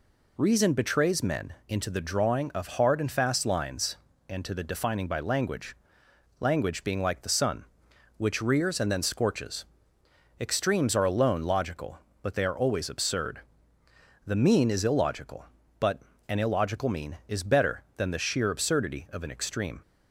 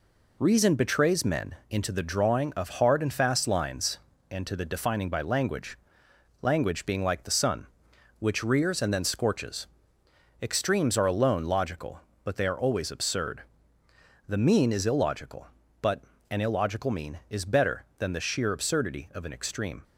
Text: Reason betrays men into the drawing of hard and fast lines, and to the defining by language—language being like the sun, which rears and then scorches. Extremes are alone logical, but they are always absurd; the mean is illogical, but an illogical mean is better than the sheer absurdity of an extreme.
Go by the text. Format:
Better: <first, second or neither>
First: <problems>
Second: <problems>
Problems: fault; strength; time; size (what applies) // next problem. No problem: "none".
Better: first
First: pauses between "men" and "into"; slight; at 1.5 s; 0.16 s long // pauses between "but" and "an"; slight; at 16.0 s; 0.30 s long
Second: gets quieter; noticeable; throughout; 5 dB // pauses between "men" and "into"; slight; at 1.5 s; 0.16 s long // pauses between "but" and "an"; slight; at 16.0 s; 0.30 s long